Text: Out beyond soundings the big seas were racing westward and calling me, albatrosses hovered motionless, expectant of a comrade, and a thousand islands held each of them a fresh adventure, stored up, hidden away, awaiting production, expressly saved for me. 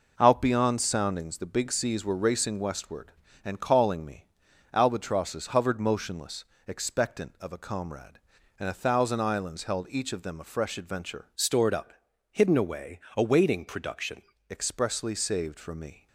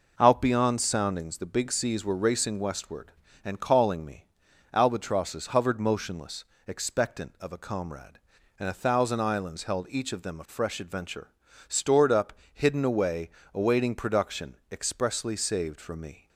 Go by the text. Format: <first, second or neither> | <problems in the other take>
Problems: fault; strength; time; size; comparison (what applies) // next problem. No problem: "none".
second | changes voice from "stored" to "production"; from 11.3 to 14.2 s; 2.9 s long